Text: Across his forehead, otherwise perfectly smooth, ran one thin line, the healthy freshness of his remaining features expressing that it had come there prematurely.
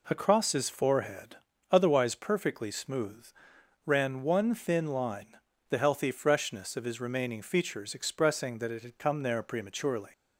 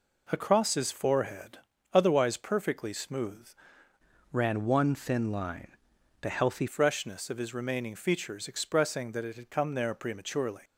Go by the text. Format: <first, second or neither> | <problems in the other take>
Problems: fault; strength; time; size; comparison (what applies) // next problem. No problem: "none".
first | changes voice from "ran" to "healthy"; from 4.3 to 6.6 s; 2.3 s long